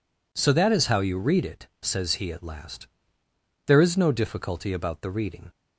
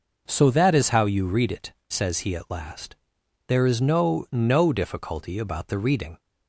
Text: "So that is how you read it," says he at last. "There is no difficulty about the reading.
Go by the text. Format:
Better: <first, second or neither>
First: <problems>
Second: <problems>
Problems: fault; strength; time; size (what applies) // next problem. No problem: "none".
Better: first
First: none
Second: says "no" twice; at 4.3 s